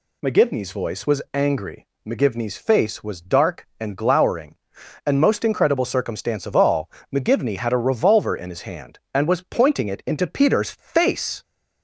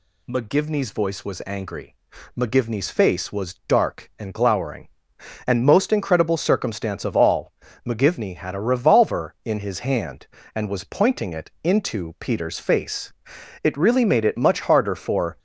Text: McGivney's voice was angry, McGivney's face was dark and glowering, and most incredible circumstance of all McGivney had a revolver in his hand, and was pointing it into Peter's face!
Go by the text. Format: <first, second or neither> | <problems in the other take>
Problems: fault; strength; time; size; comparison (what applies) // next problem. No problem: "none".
first | pauses between "all" and "McGivney"; slight; at 7.5 s; 0.34 s long; slight in the first // goes on to say "It really made it much harder for"; strong; from 13.6 s on; 1.7 s long